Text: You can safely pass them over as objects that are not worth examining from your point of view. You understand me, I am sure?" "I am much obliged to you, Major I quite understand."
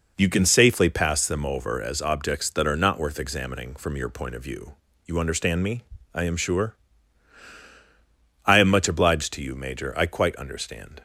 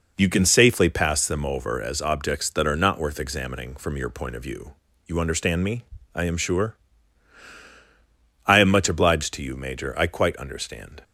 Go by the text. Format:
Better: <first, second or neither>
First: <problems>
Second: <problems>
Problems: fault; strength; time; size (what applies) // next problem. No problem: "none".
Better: neither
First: none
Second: none